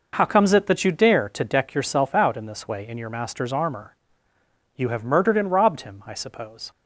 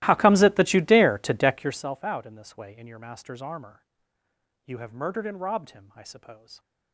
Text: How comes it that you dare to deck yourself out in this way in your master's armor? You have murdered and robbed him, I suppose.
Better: first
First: none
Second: starts louder than the rest; strong; until 1.8 s; 16.5 dB

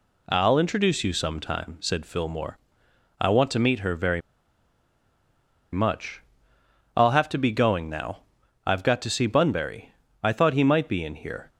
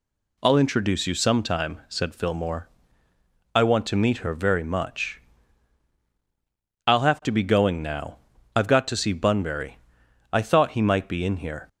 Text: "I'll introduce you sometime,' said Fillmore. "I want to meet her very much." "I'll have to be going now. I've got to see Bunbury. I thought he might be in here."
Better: second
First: pauses between "very" and "much"; strong; at 4.2 s; 1.5 s long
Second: none

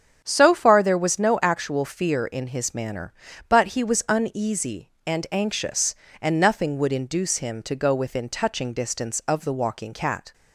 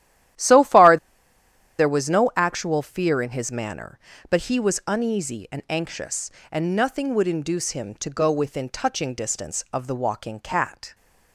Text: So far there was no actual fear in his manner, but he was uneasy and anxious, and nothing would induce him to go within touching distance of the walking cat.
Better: first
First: starts louder than the rest; strong; until 1.2 s; 8.5 dB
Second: starts louder than the rest; strong; until 2.1 s; 12.5 dB // pauses between "far" and "there"; noticeable; at 0.9 s; 0.81 s long

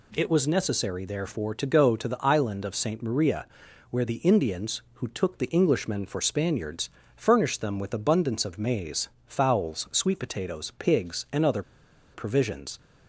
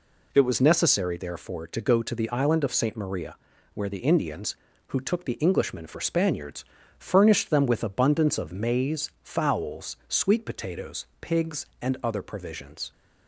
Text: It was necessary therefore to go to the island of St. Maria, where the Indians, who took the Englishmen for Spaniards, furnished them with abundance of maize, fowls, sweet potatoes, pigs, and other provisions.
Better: second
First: pauses between "other" and "provisions"; noticeable; at 11.6 s; 0.52 s long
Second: none

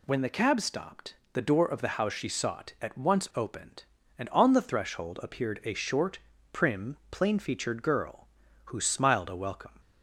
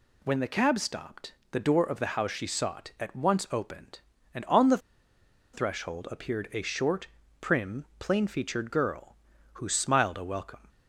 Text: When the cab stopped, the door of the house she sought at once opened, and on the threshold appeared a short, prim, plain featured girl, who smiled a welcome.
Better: first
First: none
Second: pauses between "the" and "threshold"; noticeable; at 4.7 s; 0.75 s long

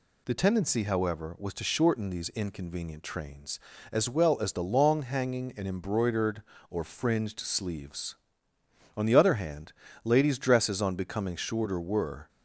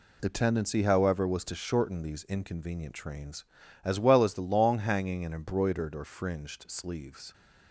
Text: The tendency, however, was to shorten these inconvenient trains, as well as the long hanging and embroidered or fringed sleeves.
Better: second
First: goes on to say "On the other hand ladies dresses on becoming shorter were"; strong; from 8.9 s on; 3.3 s long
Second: none

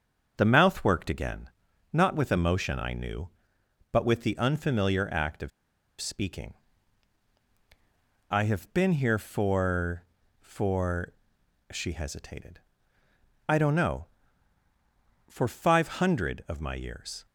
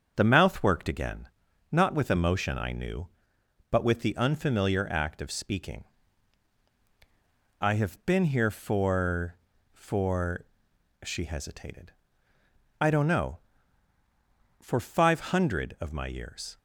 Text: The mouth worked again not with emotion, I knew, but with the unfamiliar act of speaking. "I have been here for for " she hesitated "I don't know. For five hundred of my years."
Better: second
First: starts louder than the rest; strong; until 1.3 s; 7.5 dB // pauses between "again" and "not"; noticeable; at 1.4 s; 0.46 s long // pauses between "of" and "speaking"; noticeable; at 5.5 s; 0.51 s long // pauses between "hesitated" and "I"; noticeable; at 12.6 s; 0.86 s long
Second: starts louder than the rest; strong; until 1.1 s; 7.5 dB // pauses between "again" and "not"; noticeable; at 1.2 s; 0.46 s long // pauses between "hesitated" and "I"; noticeable; at 11.9 s; 0.86 s long

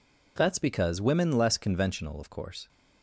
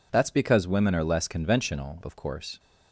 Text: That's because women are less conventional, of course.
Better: second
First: skips "are"; at 1.3 s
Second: none

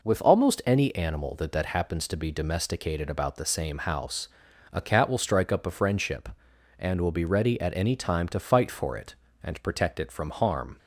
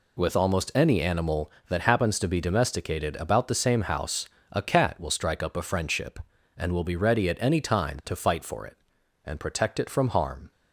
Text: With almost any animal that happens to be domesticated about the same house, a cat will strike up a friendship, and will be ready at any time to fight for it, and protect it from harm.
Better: second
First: says "that" twice; at 1.5 s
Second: none

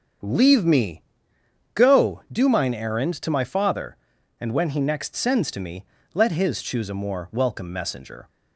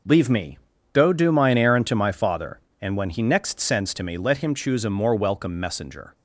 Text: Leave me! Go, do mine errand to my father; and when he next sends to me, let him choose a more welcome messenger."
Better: second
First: starts louder than the rest; until 1.9 s; 7 dB // says "his" for "him"; at 6.3 s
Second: none

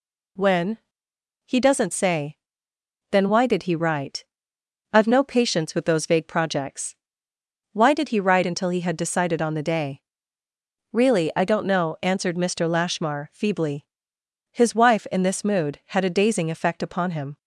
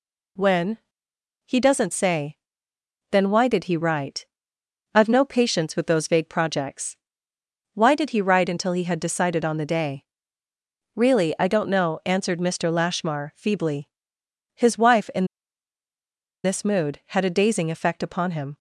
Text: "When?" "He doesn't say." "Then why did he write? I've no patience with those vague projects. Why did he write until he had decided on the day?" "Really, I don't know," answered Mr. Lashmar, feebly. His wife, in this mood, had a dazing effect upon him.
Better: first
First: none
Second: pauses between "in" and "this"; at 15.2 s; 1.1 s long

